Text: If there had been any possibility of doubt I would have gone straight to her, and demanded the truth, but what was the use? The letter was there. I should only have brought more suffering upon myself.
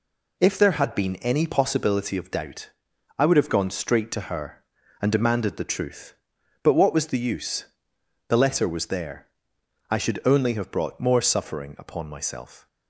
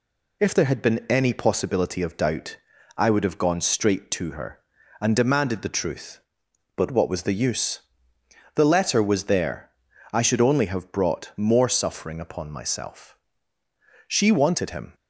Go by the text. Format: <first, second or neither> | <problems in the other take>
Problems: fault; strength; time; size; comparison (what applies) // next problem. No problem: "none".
first | pauses between "doubt" and "I"; at 2.5 s; 0.40 s long; noticeable in the first // goes on to say "She wanted him"; noticeable; from 14.0 s on; 0.88 s long